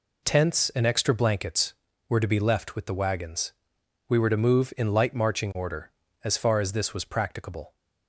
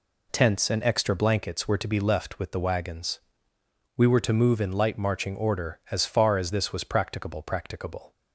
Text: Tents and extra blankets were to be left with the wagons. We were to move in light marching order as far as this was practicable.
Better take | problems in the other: first | says "practicable" twice; at 7.4 s

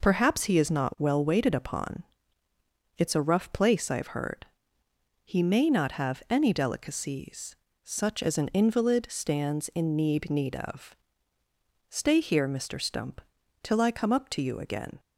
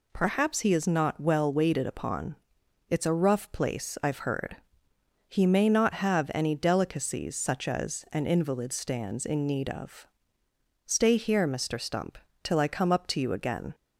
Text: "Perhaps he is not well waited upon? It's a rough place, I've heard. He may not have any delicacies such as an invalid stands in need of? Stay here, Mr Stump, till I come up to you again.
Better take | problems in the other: second | pauses between "delicacies" and "such"; slight; at 7.5 s; 0.30 s long // says "need" twice; at 10.2 s

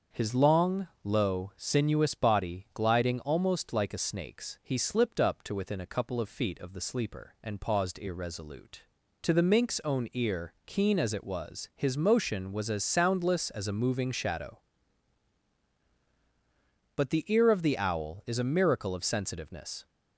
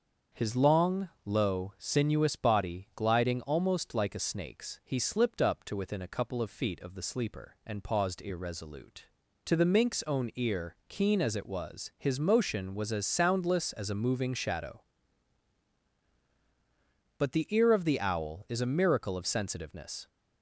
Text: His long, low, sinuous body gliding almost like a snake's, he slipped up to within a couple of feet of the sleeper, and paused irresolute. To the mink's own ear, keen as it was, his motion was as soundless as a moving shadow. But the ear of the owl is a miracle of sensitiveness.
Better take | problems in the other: neither | starts louder than the rest; the same in both

